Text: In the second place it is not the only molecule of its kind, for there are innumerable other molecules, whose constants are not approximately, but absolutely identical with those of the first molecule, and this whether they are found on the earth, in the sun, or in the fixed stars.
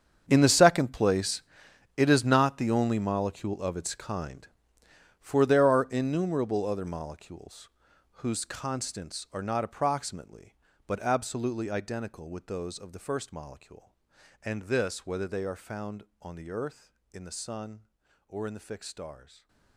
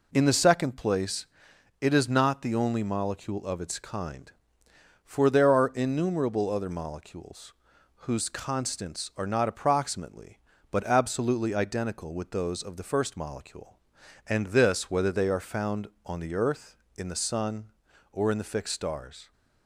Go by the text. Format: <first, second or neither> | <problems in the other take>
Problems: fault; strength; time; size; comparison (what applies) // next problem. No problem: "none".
second | gets quieter; strong; throughout; 17.5 dB // pauses between "place" and "it"; noticeable; at 1.4 s; 0.54 s long; noticeable in the second // stays silent after the last word; slight; from 19.2 s on; 0.5 s long